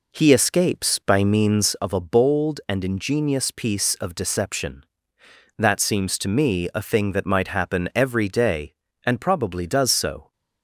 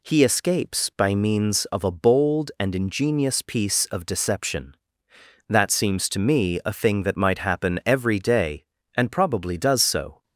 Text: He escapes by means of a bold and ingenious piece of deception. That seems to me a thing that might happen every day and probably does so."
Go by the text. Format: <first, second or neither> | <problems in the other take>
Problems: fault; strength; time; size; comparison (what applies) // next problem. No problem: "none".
second | starts louder than the rest; until 1.8 s; 3.5 dB